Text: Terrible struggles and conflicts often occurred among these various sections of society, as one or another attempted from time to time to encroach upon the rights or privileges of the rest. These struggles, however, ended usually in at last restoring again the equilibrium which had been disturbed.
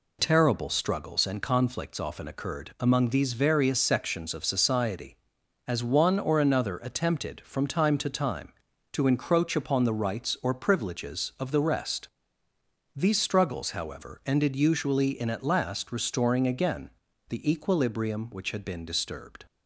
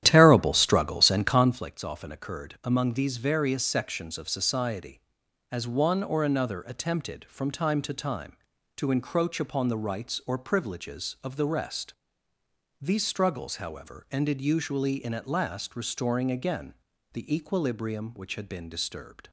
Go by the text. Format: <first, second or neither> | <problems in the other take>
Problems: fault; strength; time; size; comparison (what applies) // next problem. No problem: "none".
first | starts louder than the rest; strong; until 1.7 s; 11.5 dB // pauses between "again" and "the"; at 16.7 s; 0.38 s long; also in the first